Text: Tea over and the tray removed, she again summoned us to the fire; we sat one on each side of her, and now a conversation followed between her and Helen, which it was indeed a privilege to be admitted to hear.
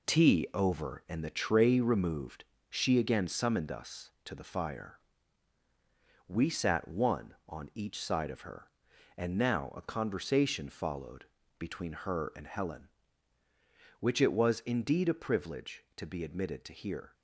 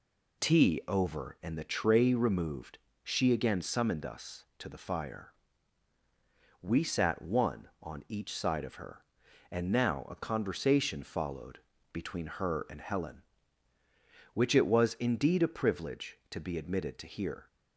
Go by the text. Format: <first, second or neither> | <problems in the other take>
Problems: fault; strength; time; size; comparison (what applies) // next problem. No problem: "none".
second | gets quieter; throughout; 7 dB // pauses between "followed" and "between"; slight; at 11.2 s; 0.32 s long; slight in the second